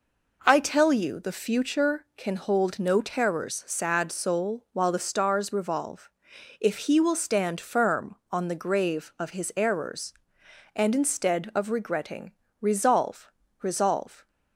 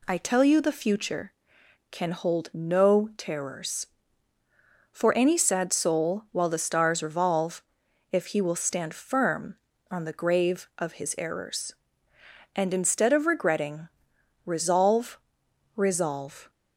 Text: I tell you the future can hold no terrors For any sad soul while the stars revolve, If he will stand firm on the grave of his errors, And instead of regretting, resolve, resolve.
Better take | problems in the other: second | skips "For any"; at 3.6 s

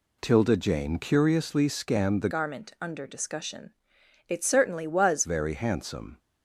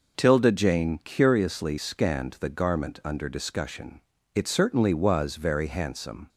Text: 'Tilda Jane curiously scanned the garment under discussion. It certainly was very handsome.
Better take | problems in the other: second | changes voice from "garment" to "was"; from 2.2 to 5.2 s; 3.0 s long

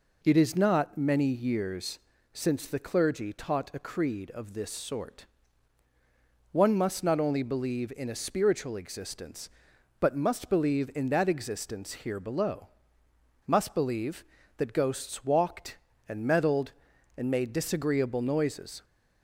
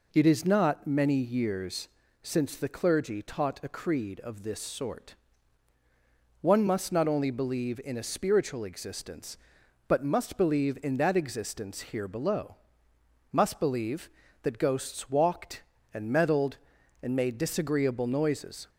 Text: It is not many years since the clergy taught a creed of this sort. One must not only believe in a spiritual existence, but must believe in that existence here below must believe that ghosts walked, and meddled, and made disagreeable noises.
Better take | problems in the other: neither | pauses between "years" and "since"; slight; the same in both // pauses between "below" and "must"; noticeable; the same in both

